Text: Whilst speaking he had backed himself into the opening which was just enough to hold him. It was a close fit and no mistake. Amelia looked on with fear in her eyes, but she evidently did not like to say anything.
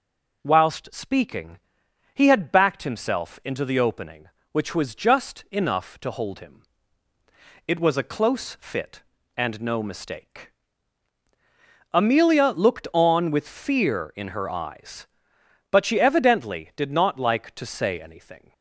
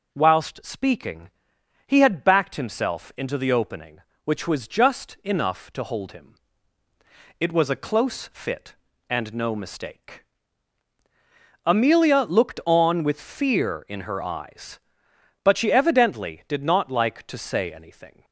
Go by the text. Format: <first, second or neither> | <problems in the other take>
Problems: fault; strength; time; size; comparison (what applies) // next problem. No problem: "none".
neither | pauses between "speaking" and "he"; noticeable; the same in both